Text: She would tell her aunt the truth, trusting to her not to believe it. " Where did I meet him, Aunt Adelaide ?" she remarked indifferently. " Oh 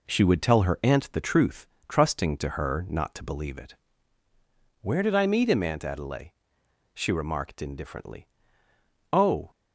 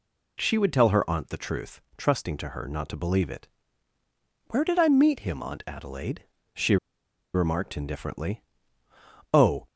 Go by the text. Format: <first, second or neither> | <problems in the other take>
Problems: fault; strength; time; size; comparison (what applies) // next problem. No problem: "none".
first | pauses between "she" and "remarked"; noticeable; at 6.7 s; 0.57 s long